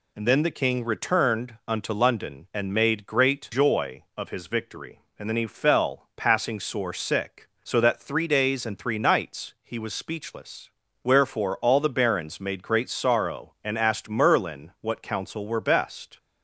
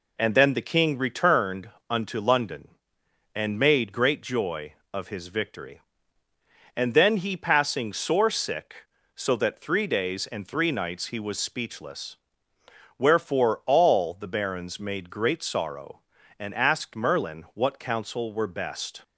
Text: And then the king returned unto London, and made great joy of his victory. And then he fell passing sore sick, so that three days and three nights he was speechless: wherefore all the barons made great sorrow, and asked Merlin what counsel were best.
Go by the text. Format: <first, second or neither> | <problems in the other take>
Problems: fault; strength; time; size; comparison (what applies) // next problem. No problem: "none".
first | pauses between "returned" and "unto"; slight; at 1.6 s; 0.20 s long // skips "fell"; at 7.3 s